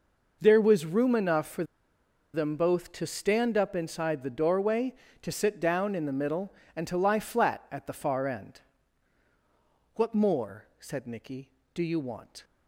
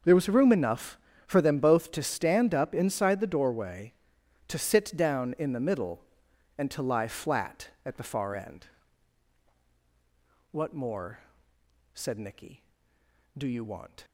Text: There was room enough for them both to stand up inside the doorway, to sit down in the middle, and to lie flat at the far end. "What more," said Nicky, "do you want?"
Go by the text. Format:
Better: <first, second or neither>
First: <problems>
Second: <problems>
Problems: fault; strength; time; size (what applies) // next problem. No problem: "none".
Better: second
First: pauses between "for" and "them"; noticeable; at 1.6 s; 0.69 s long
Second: none